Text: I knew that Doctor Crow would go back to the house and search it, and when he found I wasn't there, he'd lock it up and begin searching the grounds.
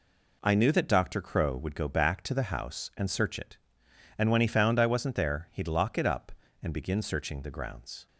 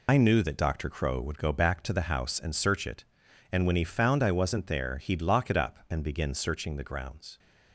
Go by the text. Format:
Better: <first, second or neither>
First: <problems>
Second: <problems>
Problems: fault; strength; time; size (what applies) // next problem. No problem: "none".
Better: first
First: none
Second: loses the start of "I"; at 0.0 s; 50 ms